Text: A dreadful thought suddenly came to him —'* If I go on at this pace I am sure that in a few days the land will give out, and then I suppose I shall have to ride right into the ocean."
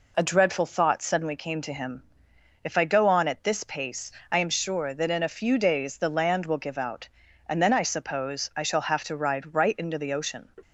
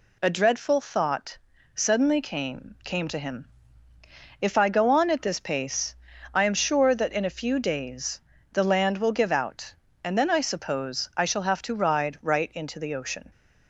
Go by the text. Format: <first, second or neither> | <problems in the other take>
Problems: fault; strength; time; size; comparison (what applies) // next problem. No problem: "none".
first | pauses between "thought" and "suddenly"; at 1.3 s; 0.38 s long // says "came" twice; at 2.8 s // pauses between "pace" and "I"; at 5.9 s; 0.40 s long; slight in the first // pauses between "days" and "the"; slight; at 8.2 s; 0.30 s long